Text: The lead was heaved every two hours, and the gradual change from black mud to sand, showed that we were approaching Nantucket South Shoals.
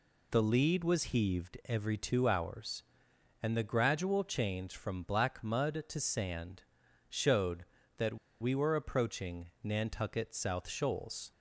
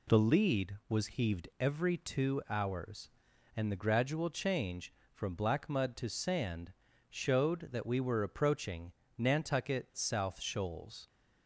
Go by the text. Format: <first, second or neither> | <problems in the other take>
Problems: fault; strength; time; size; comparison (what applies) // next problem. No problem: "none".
second | pauses between "that" and "we"; slight; at 8.1 s; 0.25 s long // pauses between "approaching" and "Nantucket"; slight; at 9.4 s; 0.18 s long; slight in the second